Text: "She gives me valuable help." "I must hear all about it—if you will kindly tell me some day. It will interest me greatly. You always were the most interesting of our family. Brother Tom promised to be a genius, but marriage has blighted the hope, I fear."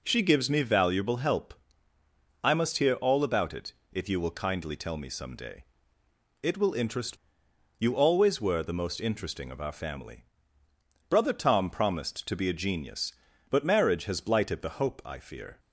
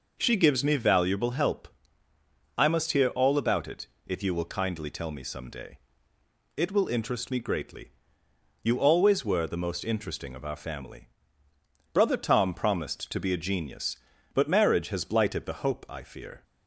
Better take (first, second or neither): second